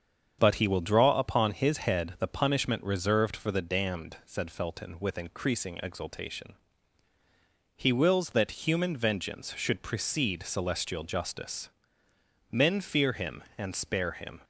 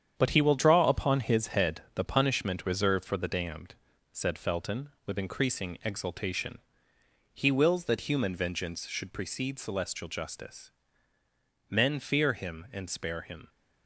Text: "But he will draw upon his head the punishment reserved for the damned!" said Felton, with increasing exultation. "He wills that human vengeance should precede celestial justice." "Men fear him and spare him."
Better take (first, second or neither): first